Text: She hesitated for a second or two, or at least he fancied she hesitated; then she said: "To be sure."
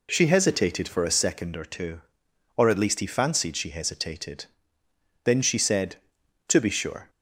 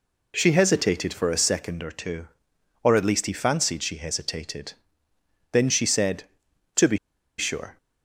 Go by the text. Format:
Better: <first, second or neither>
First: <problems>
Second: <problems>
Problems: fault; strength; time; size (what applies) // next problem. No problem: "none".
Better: first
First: none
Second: pauses between "be" and "sure"; at 6.9 s; 0.41 s long